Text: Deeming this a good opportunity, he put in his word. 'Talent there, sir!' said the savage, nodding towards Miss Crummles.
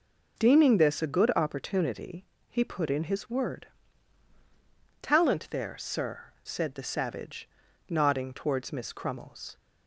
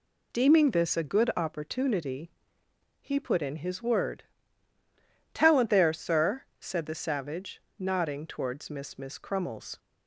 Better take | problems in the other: first | says "Miss" twice; at 8.9 s

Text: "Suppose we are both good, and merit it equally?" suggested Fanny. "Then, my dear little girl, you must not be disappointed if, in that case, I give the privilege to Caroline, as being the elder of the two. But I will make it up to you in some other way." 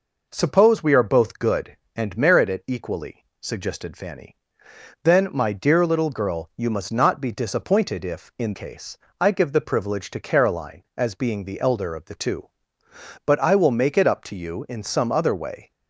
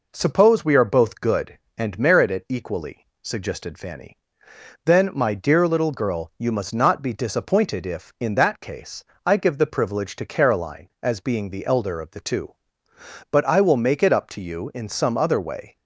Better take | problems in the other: second | skips "that"; at 8.5 s

